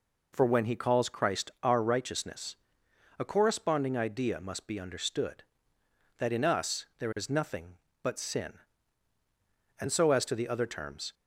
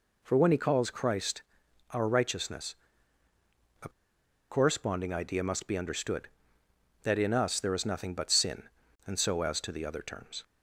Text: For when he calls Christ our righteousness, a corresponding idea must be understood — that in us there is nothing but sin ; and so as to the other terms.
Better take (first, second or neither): first